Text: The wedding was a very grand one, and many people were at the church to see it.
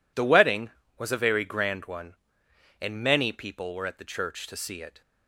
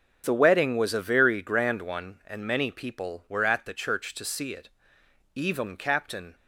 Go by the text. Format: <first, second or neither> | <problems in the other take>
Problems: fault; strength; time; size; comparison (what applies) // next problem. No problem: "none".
first | starts louder than the rest; until 1.2 s; 6.5 dB // goes on to say "Even Captain"; noticeable; from 5.3 s on; 1.0 s long